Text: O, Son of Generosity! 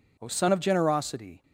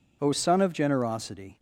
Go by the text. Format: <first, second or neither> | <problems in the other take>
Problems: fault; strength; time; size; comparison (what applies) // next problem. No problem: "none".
neither | none